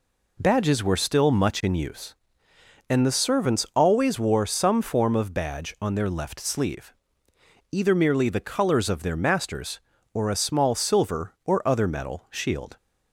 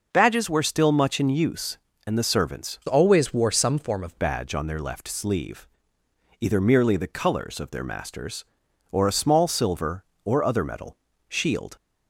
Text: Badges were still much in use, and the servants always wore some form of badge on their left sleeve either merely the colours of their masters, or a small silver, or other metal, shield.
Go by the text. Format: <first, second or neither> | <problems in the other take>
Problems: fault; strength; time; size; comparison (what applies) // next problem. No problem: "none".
first | changes voice from "always" to "of"; from 2.8 to 4.1 s; 1.3 s long // pauses between "sleeve" and "either"; noticeable; at 5.6 s; 0.76 s long; noticeable in the first